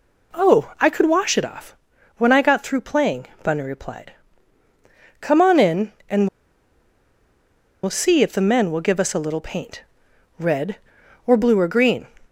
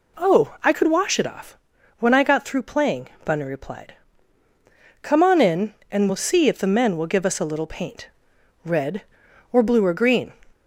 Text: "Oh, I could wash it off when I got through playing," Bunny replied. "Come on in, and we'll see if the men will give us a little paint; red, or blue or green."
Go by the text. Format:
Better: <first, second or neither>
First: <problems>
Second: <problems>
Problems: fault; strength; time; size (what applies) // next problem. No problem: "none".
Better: second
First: pauses between "off" and "when"; at 1.7 s; 0.42 s long // pauses between "and" and "we'll"; strong; at 6.2 s; 1.5 s long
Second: pauses between "off" and "when"; at 1.5 s; 0.42 s long